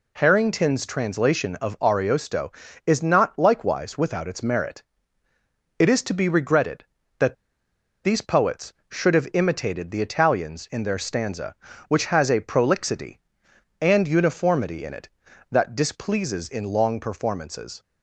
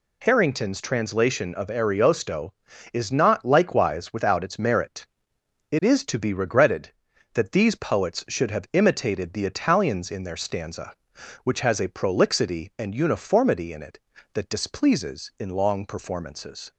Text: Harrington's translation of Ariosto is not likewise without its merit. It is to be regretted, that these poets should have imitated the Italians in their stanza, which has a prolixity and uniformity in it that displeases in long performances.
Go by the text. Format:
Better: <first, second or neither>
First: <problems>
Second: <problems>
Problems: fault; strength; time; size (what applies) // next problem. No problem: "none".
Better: second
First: pauses between "that" and "these"; noticeable; at 7.3 s; 0.68 s long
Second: none